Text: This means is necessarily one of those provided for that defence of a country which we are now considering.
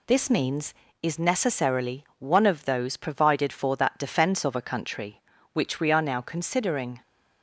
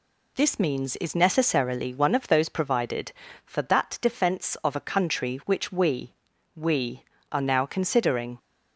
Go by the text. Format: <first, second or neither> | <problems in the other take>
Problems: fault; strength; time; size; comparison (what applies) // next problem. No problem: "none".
first | says "we" twice; at 6.5 s